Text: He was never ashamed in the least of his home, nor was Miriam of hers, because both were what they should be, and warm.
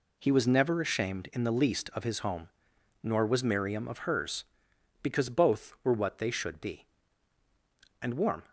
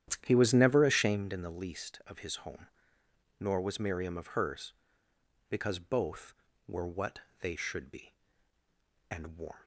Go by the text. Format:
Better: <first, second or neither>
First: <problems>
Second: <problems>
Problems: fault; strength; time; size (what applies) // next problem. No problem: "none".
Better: first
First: none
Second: starts louder than the rest; strong; until 1.2 s; 10.5 dB // pauses between "what" and "they"; slight; at 7.1 s; 0.22 s long